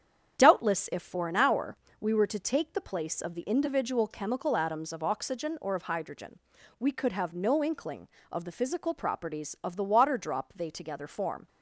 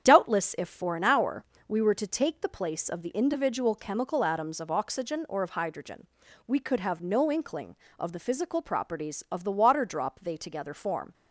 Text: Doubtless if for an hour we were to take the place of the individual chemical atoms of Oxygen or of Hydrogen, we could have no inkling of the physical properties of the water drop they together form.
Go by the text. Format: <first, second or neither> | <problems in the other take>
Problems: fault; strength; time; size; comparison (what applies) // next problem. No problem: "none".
neither | starts louder than the rest; strong; the same in both // pauses between "hour" and "we"; slight; the same in both